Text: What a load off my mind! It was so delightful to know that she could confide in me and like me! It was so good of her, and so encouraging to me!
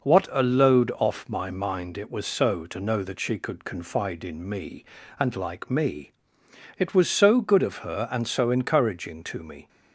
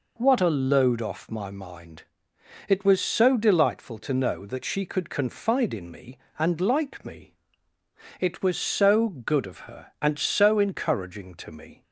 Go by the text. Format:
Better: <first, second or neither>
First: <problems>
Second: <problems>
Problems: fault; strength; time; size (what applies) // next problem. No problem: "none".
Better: second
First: skips "delightful"; at 2.6 s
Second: none